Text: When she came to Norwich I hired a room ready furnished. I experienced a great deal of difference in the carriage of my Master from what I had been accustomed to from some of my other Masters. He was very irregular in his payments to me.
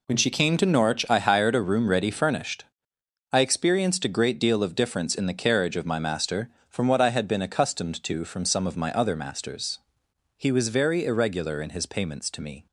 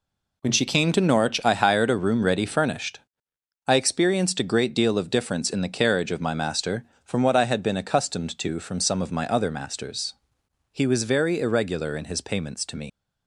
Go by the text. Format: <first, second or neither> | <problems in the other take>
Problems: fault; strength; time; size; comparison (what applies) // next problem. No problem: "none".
first | leaves "me" unfinished; at 12.8 s; 115 ms